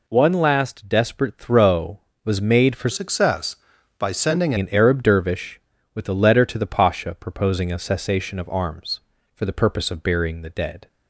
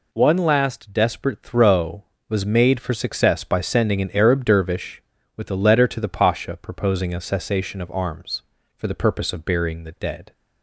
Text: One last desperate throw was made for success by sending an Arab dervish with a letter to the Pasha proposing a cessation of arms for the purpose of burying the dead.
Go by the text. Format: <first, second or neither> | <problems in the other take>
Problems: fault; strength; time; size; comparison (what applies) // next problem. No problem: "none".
second | changes voice from "success" to "sending"; from 2.9 to 4.5 s; 1.6 s long